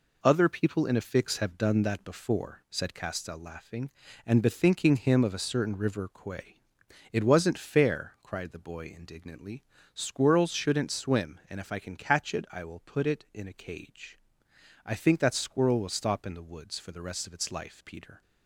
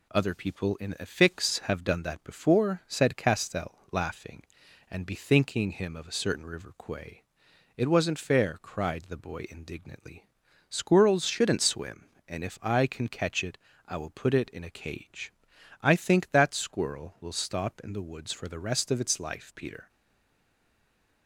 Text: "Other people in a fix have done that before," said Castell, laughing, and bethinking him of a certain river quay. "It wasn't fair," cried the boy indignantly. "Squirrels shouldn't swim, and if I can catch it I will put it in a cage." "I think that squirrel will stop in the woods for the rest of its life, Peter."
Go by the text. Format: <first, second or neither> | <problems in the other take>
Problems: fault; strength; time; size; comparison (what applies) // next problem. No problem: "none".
first | pauses between "it" and "I"; slight; at 13.5 s; 0.32 s long // stays silent after the last word; noticeable; from 19.8 s on; 1.4 s long